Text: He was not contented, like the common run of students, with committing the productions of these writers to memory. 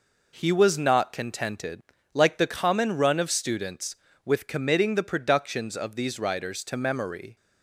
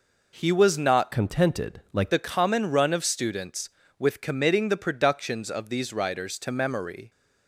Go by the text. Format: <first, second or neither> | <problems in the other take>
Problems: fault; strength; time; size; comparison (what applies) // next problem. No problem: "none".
first | changes voice from "contented" to "like"; from 1.1 to 2.1 s; 1.0 s long